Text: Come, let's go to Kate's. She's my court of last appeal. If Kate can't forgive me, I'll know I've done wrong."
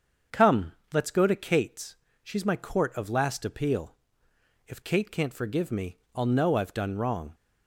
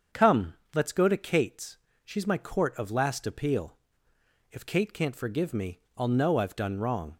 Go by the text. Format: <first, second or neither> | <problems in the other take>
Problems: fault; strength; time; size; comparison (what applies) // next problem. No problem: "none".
neither | starts louder than the rest; the same in both